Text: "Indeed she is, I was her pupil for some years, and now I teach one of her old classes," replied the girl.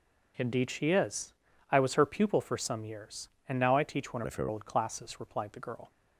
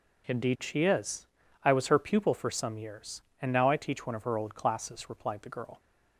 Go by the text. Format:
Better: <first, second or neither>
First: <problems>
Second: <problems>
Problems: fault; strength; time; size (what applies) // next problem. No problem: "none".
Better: second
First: changes voice from "of" to "her"; from 4.2 to 4.4 s; 0.2 s long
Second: none